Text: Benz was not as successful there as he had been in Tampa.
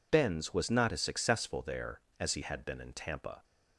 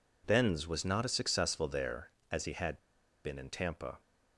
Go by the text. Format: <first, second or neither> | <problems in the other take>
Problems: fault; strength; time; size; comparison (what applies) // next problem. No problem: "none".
first | pauses between "had" and "been"; at 2.7 s; 0.45 s long